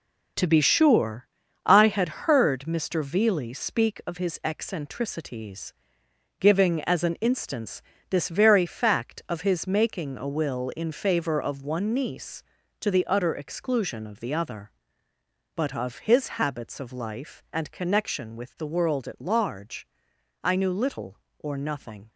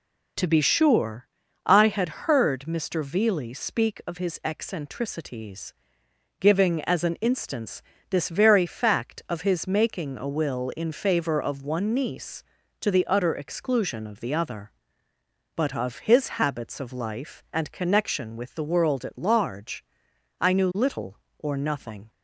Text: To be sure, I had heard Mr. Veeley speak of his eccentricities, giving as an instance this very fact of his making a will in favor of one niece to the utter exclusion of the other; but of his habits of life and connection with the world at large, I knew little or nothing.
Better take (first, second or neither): second